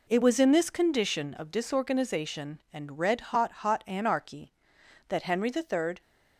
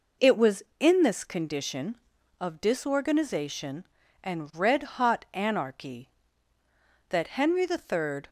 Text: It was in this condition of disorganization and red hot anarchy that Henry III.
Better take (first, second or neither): second